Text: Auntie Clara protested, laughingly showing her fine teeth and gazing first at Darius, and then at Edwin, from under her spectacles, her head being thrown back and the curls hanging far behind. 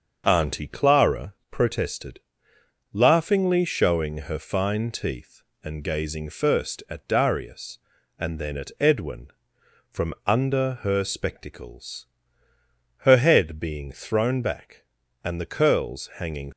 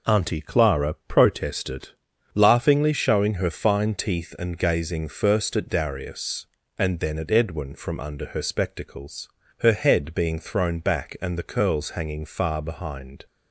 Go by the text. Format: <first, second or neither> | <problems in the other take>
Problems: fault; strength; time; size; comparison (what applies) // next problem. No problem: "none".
second | starts louder than the rest; until 1.2 s; 6.5 dB // pauses between "Clara" and "protested"; slight; at 1.3 s; 0.16 s long // stops before "far behind"; at 16.5 s